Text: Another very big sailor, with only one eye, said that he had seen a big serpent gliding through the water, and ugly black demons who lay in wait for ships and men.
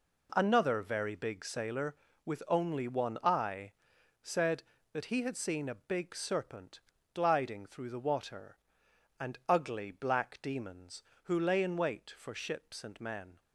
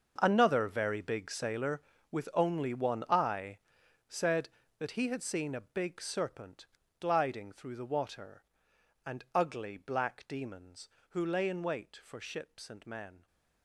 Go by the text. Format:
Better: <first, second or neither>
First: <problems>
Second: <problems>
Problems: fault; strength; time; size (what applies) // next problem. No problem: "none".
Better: first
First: pauses between "serpent" and "gliding"; slight; at 6.7 s; 0.36 s long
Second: gets quieter; strong; throughout; 15 dB // pauses between "serpent" and "gliding"; slight; at 6.6 s; 0.36 s long